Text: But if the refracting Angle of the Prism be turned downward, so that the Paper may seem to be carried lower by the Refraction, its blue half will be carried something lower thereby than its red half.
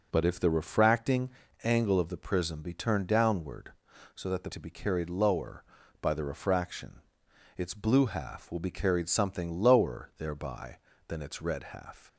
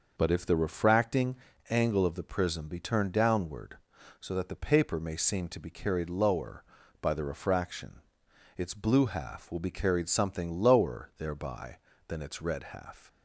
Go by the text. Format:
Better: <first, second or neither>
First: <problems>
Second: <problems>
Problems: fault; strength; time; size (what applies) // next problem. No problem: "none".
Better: second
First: pauses between "refracting" and "Angle"; slight; at 1.2 s; 0.34 s long // skips "Paper may seem"; at 4.5 s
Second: pauses between "refracting" and "Angle"; slight; at 1.3 s; 0.34 s long